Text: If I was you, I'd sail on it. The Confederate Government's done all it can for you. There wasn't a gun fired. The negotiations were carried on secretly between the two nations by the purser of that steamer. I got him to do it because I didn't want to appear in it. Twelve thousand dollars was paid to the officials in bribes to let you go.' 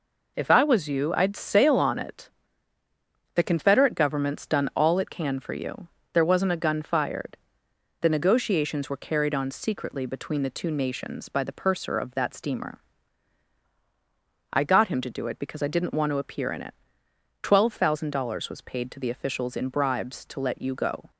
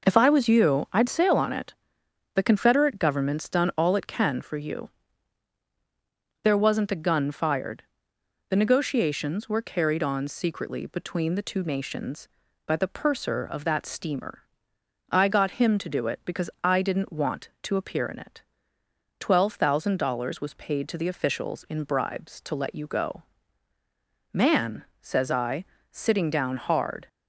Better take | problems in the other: first | goes on to say "Man says I sitting down hard"; strong; from 24.3 s on; 2.7 s long

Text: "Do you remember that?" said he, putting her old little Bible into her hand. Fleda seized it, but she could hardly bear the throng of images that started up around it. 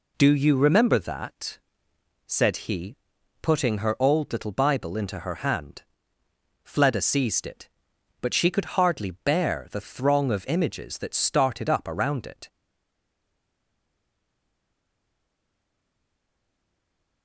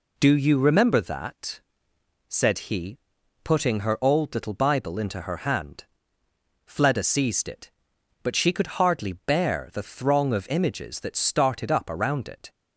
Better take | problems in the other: second | stays silent after the last word; strong; from 12.4 s on; 4.8 s long

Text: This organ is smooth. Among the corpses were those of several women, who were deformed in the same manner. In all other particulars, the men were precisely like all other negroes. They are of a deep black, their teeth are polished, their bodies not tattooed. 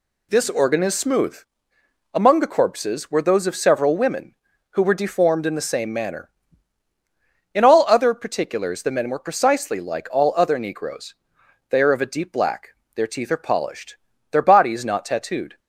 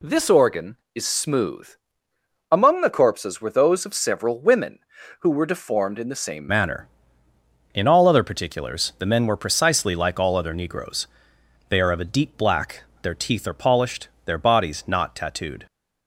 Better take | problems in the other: first | changes voice at "manner"; from 6.4 s on; 9.2 s long

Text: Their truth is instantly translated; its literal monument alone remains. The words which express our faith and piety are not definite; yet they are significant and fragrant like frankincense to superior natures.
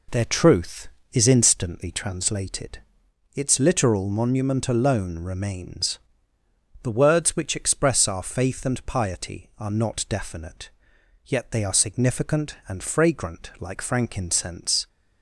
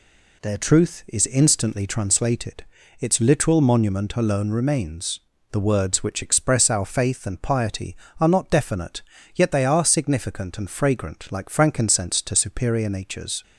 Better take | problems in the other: second | stops before "to superior natures"; at 14.8 s

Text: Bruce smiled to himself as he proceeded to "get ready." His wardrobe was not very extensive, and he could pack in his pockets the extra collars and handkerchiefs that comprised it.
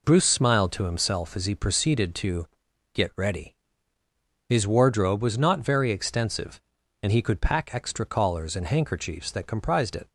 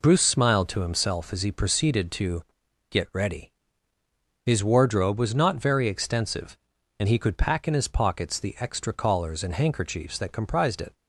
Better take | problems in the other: second | pauses between "to" and "get"; noticeable; at 2.4 s; 0.48 s long; noticeable in the second // skips "in his pockets the"; at 7.6 s

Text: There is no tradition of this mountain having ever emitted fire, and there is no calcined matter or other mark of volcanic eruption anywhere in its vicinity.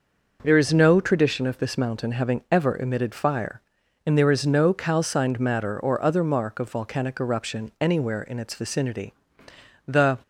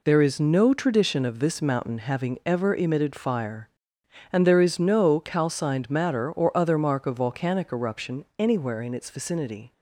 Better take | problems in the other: second | goes on to say "The"; slight; from 9.8 s on; 0.30 s long

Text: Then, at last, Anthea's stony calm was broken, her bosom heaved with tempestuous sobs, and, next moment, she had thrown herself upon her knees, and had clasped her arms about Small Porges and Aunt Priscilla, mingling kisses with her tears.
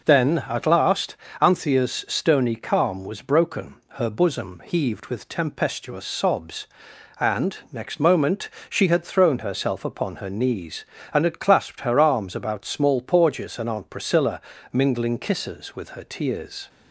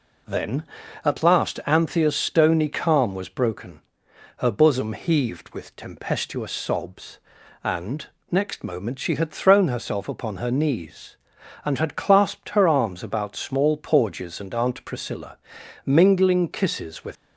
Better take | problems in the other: first | stops before "her tears"; at 17.1 s

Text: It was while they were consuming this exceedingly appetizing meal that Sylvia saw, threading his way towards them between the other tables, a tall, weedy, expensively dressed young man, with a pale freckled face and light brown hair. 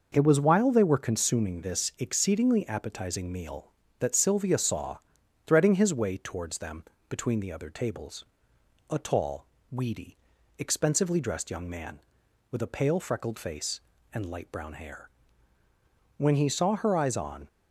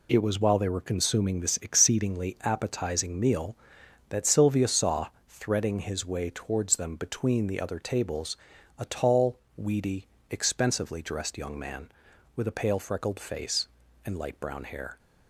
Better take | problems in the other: second | pauses between "them" and "between"; slight; at 6.8 s; 0.26 s long // goes on to say "When he saw her eyes on"; noticeable; from 16.1 s on; 1.3 s long

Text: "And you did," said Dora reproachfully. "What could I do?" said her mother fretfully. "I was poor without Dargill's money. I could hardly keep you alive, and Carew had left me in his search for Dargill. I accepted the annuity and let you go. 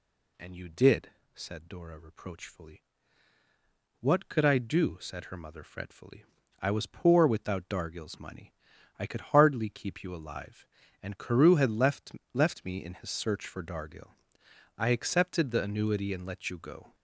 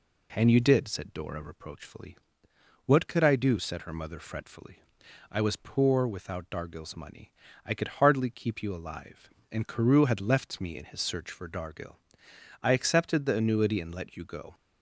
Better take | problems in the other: second | says "left" twice; at 12.3 s

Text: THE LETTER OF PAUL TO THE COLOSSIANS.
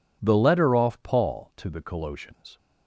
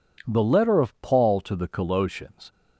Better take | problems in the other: second | says "Off" for "OF"; at 0.7 s

